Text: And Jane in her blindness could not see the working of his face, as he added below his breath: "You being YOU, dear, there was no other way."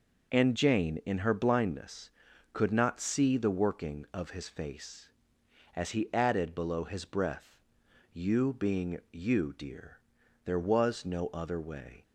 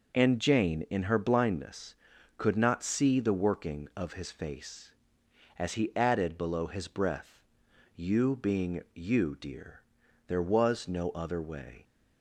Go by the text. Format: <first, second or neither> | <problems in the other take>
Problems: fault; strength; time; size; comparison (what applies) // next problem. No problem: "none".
neither | none